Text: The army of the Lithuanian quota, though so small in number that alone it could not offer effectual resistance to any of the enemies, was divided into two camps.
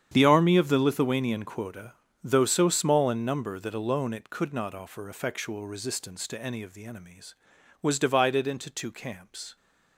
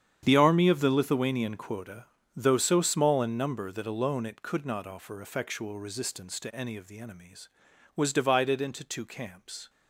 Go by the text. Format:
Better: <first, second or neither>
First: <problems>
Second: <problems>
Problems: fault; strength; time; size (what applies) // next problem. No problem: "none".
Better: neither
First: starts louder than the rest; strong; until 1.1 s; 8.5 dB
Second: starts louder than the rest; strong; until 1.2 s; 8.5 dB